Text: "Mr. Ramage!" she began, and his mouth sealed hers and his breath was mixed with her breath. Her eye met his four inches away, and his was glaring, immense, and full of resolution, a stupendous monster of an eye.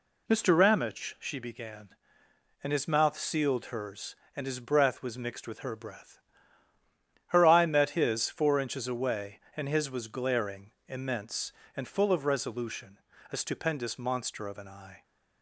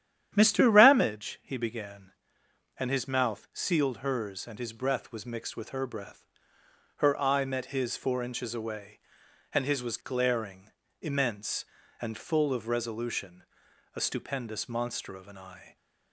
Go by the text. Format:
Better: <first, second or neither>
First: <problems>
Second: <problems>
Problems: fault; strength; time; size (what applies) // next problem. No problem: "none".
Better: first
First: none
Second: starts louder than the rest; strong; until 1.3 s; 10 dB // says "he" for "she"; at 1.4 s